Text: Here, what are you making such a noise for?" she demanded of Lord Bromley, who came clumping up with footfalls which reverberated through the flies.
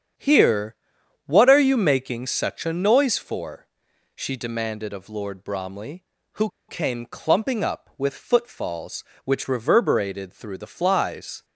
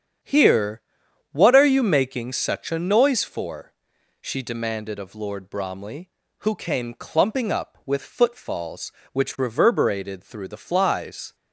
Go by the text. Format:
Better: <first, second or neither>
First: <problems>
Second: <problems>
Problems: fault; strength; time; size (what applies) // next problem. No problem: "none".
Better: second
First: starts louder than the rest; strong; until 1.6 s; 8 dB // pauses between "who" and "came"; slight; at 6.4 s; 0.19 s long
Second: starts louder than the rest; strong; until 1.7 s; 8 dB